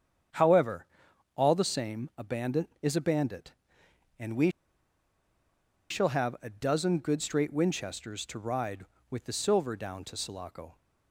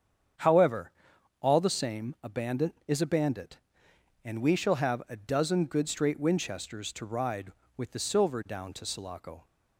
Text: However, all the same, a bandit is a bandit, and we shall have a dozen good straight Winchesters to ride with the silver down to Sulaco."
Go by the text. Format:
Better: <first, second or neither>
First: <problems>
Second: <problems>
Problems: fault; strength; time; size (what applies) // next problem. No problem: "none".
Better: second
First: starts louder than the rest; strong; until 1.8 s; 8 dB // pauses between "we" and "shall"; strong; at 4.5 s; 1.3 s long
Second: starts louder than the rest; strong; until 1.8 s; 8 dB